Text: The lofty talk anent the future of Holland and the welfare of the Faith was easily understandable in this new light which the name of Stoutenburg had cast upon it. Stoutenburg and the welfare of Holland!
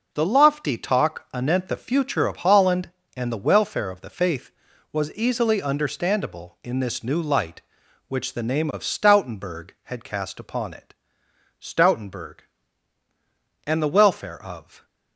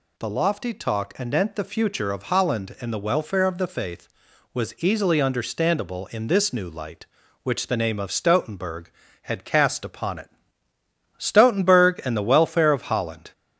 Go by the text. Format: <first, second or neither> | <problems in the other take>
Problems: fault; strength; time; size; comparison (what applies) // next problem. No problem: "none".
second | stops before "Holland"; at 14.8 s